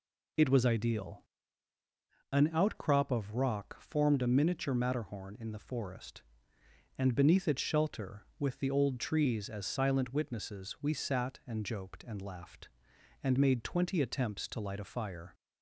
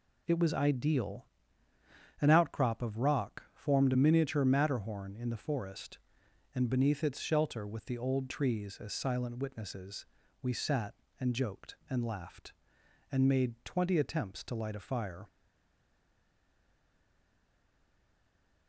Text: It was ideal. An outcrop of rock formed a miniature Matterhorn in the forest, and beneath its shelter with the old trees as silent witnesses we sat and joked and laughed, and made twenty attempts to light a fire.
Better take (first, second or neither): first